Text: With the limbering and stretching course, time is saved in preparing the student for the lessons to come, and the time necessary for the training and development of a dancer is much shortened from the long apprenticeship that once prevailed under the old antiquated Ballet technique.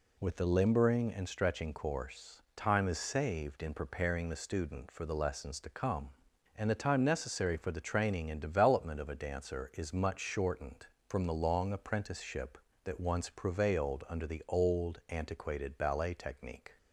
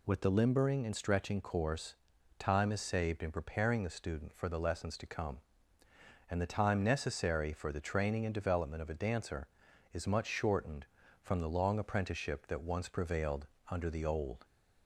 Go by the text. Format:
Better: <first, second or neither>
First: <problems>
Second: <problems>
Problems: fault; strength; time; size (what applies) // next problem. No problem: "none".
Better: first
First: none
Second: pauses between "prevailed" and "under"; slight; at 13.4 s; 0.24 s long // stops before "antiquated Ballet technique"; at 14.4 s